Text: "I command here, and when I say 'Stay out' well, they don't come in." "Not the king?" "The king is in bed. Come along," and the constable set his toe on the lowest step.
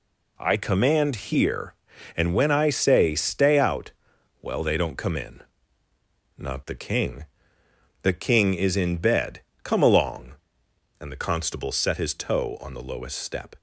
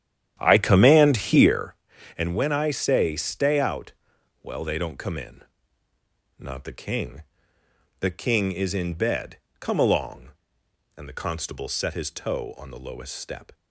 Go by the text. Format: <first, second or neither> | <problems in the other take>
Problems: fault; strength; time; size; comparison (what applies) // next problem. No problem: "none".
first | starts louder than the rest; strong; until 1.7 s; 10 dB // pauses between "out" and "well"; noticeable; at 3.9 s; 0.50 s long; noticeable in the first